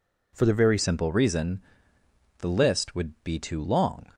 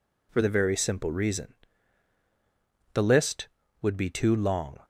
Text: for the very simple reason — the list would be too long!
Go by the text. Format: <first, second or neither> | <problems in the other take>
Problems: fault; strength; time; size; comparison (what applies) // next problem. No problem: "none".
second | changes voice at "simple"; from 0.7 s on; 3.3 s long